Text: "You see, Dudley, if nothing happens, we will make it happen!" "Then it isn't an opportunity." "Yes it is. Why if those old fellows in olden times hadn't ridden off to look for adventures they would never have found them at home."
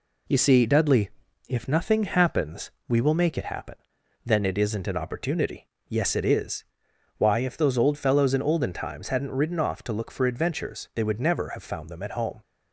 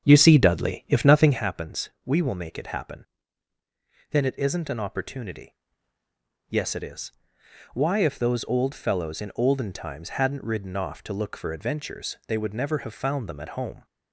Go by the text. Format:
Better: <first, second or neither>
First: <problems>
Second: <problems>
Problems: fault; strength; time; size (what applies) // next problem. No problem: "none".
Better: first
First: none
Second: starts louder than the rest; strong; until 1.4 s; 8 dB